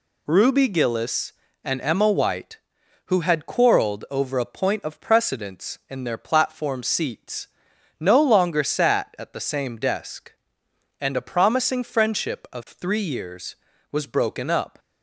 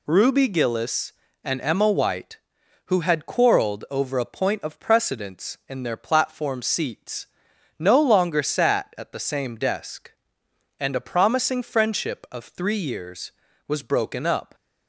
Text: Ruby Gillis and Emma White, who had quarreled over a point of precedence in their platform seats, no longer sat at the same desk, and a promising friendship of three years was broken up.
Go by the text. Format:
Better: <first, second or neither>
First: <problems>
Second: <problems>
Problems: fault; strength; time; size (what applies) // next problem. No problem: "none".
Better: neither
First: none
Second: none